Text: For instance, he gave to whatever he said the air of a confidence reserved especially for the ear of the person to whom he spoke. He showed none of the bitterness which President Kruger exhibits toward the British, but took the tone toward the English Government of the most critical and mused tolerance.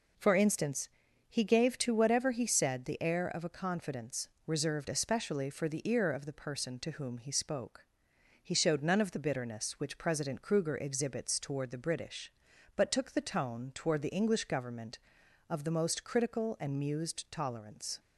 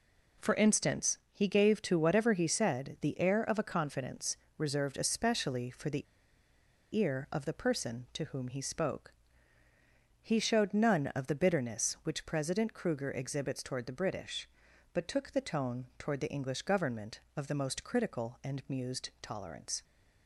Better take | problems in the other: first | pauses between "confidence" and "reserved"; slight; at 4.3 s; 0.20 s long; slight in the first // pauses between "the" and "ear"; noticeable; at 6.0 s; 0.89 s long

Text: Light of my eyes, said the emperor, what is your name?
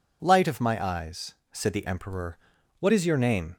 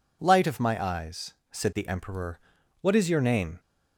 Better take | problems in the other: neither | none

